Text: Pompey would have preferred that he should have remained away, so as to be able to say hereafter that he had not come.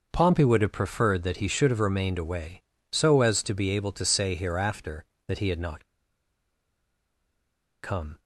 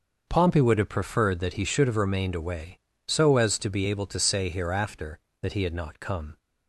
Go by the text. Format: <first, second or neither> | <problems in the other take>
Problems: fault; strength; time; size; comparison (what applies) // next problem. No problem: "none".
second | starts louder than the rest; noticeable; until 1.1 s; 6 dB; also in the second // pauses between "not" and "come"; strong; at 5.8 s; 1.9 s long